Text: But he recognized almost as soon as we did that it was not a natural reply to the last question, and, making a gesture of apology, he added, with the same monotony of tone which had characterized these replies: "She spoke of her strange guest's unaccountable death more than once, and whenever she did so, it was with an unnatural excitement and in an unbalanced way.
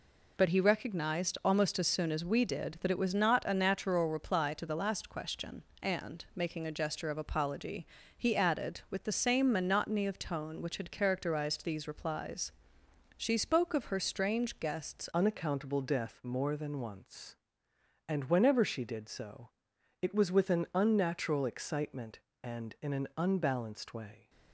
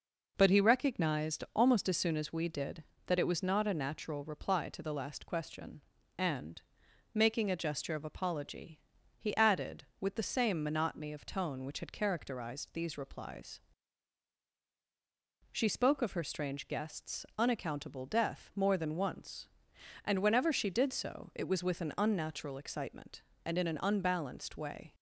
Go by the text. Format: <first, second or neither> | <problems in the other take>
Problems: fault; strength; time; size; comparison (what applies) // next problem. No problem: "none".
second | changes voice at "unaccountable"; from 15.1 s on; 9.1 s long